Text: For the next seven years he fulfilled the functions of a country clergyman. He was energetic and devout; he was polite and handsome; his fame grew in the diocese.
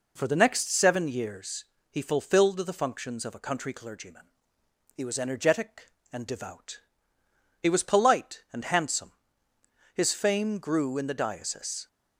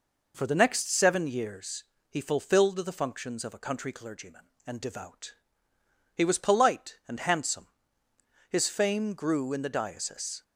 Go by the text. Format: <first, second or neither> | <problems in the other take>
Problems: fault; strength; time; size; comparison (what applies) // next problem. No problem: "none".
first | pauses between "years" and "he"; slight; at 1.8 s; 0.24 s long; slight in the first // skips "He was energetic"; at 4.5 s